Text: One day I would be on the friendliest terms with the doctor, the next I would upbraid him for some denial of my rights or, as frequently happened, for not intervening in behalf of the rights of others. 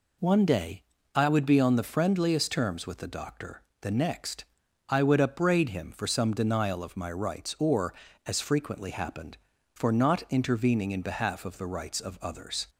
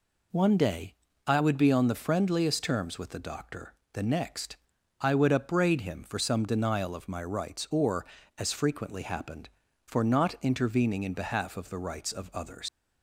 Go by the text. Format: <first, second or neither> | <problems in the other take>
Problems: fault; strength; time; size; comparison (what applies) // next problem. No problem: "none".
first | pauses between "day" and "I"; slight; at 0.9 s; 0.34 s long; slight in the first // pauses between "next" and "I"; noticeable; at 4.5 s; 0.46 s long; noticeable in the first // leaves "others" unfinished; at 12.6 s; 125 ms